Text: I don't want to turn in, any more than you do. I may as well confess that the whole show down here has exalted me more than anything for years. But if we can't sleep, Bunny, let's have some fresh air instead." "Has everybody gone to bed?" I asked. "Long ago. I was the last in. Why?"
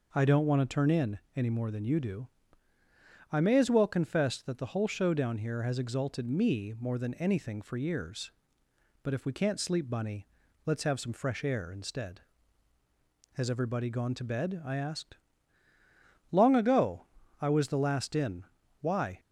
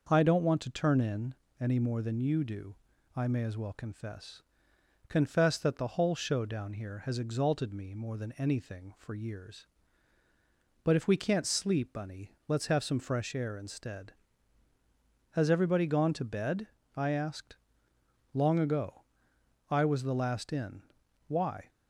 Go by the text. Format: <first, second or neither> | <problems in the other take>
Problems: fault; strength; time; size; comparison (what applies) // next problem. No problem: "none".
first | starts louder than the rest; noticeable; until 1.1 s; 6 dB // says "confess" twice; at 5.0 s